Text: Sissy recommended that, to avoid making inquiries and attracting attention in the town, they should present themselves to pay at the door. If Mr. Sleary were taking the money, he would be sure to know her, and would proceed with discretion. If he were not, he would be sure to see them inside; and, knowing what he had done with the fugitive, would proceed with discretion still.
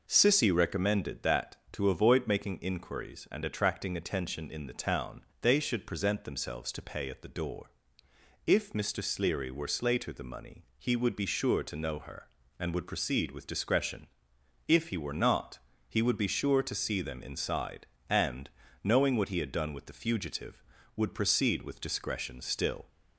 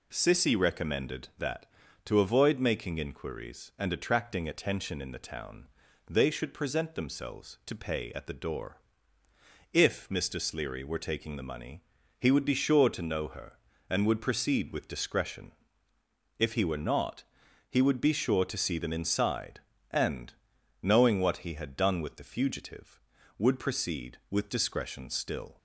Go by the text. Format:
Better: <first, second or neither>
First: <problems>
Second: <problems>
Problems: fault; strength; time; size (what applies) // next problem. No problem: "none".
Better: second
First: says "slater" for "taking"; at 9.6 s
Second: none